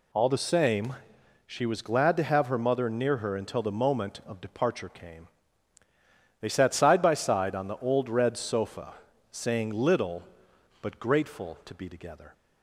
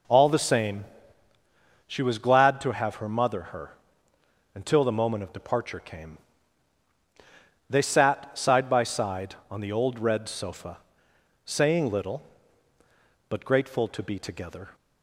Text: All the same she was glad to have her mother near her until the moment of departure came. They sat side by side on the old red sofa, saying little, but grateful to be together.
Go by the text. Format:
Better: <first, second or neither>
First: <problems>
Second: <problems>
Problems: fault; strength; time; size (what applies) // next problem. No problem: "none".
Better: first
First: pauses between "same" and "she"; noticeable; at 0.9 s; 0.52 s long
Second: pauses between "same" and "she"; at 0.8 s; 1.0 s long // skips "near"; at 3.4 s // pauses between "her" and "until"; noticeable; at 3.7 s; 0.80 s long